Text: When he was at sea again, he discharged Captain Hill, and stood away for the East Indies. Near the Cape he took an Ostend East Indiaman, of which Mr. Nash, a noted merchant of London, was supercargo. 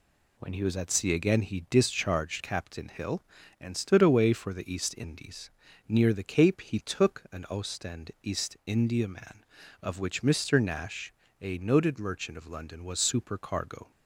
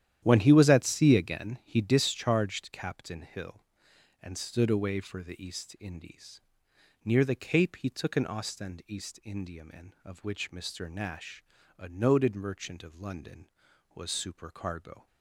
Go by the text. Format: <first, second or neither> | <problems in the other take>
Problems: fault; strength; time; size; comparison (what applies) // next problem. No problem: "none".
first | starts louder than the rest; strong; until 1.4 s; 11 dB